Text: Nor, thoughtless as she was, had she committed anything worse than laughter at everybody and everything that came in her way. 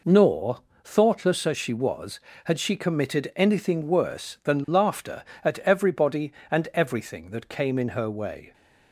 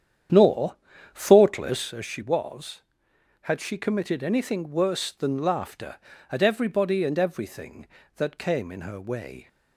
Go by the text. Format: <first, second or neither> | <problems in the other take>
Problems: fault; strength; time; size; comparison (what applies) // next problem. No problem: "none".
first | starts louder than the rest; strong; until 2.0 s; 9 dB